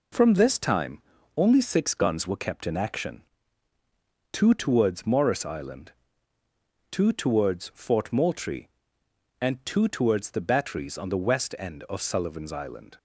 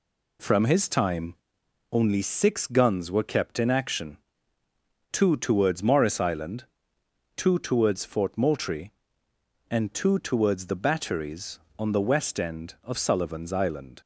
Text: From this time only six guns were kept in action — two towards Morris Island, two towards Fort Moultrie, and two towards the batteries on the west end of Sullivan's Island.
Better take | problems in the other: first | says "his" for "this"; at 0.6 s // pauses between "time" and "only"; noticeable; at 1.3 s; 0.58 s long; slight in the first

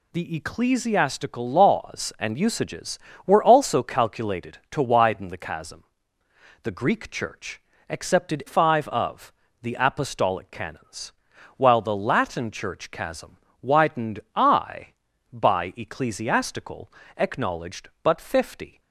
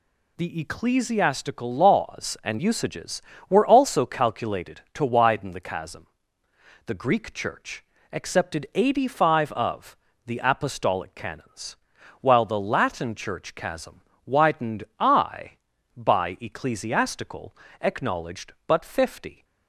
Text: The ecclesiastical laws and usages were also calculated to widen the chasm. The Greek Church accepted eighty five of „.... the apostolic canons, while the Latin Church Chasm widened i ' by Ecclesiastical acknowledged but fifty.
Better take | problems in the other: second | pauses between "Church" and "accepted"; slight; at 7.6 s; 0.28 s long; slight in the second // skips "eighty"; at 8.4 s // pauses between "Chasm" and "widened"; slight; at 13.3 s; 0.24 s long; slight in the second // pauses between "widened" and "i"; slight; at 14.1 s; 0.16 s long; slight in the second // pauses between "Ecclesiastical" and "acknowledged"; slight; at 16.9 s; 0.24 s long; slight in the second

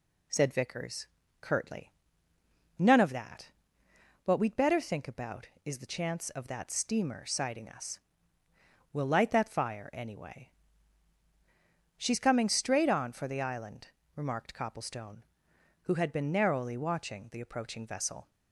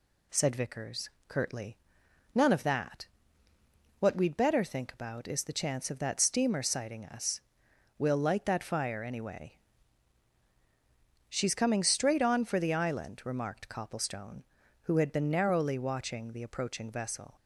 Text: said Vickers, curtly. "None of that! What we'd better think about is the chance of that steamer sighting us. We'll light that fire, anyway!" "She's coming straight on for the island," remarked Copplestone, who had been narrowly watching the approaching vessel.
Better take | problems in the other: neither | none

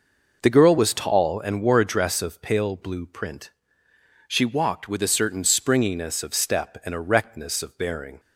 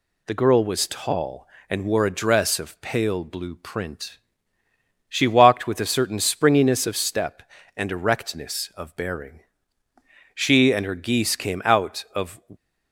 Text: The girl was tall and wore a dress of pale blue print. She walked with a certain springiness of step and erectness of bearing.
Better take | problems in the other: first | goes on to say "She and her geese came out of"; strong; from 10.3 s on; 2.0 s long

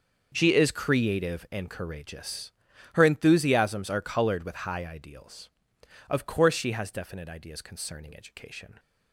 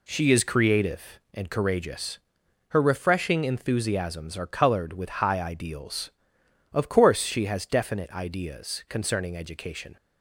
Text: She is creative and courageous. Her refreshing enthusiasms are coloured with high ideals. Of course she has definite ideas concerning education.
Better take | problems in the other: second | skips "refreshing"; at 3.0 s

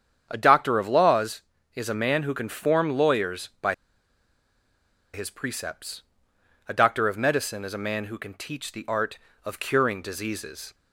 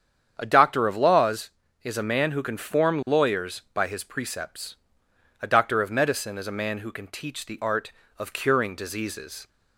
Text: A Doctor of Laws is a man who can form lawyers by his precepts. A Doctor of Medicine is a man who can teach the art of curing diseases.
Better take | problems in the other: second | starts louder than the rest; strong; until 1.3 s; 8 dB; strong in the second // pauses between "by" and "his"; strong; at 3.7 s; 1.3 s long

